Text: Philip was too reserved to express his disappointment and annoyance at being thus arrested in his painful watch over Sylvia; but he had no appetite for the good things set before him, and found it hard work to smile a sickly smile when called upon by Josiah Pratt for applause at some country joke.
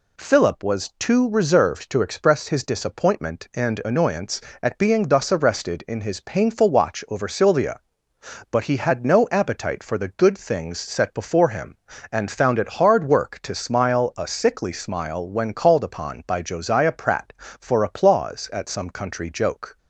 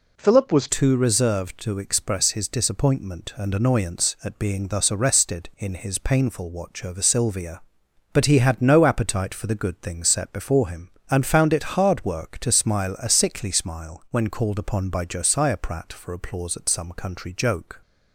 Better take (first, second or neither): first